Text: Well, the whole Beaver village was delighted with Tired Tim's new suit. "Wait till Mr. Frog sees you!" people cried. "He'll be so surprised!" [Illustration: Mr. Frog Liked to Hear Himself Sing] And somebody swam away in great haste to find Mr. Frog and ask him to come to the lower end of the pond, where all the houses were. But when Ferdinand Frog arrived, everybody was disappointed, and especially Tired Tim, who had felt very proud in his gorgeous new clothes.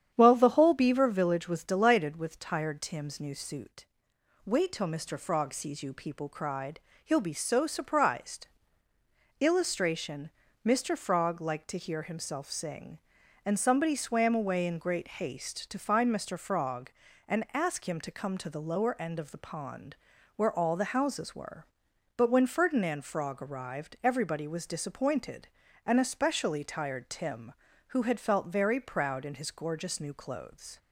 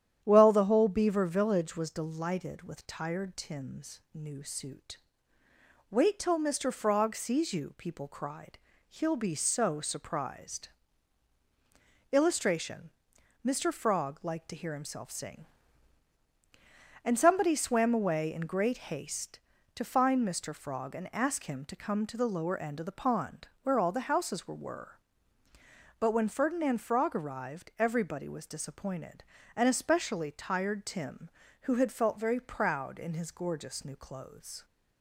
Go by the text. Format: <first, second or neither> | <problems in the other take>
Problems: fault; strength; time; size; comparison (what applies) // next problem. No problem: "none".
first | starts louder than the rest; strong; until 1.2 s; 10 dB; strong in the first // pauses between "Tim's" and "new"; slight; at 3.9 s; 0.16 s long // says "were" twice; at 24.5 s